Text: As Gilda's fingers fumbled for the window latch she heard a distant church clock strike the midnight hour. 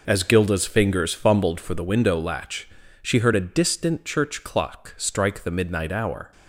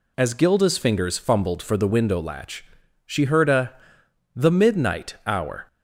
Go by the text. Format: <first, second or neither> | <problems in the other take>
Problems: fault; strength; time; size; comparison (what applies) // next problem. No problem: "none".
first | pauses between "latch" and "she"; at 2.6 s; 0.42 s long; slight in the first // skips "distant church clock strike"; at 4.0 s